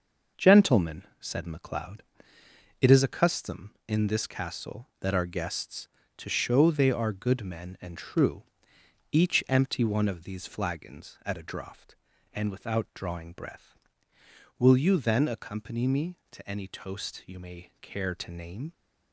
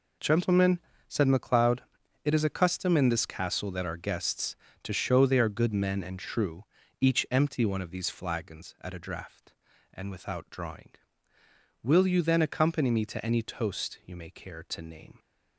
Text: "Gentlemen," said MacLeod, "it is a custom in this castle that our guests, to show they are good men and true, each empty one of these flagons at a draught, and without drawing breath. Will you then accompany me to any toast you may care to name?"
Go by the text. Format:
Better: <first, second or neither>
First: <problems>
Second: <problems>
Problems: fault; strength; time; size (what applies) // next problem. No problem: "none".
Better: first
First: none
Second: skips "breath"; at 11.3 s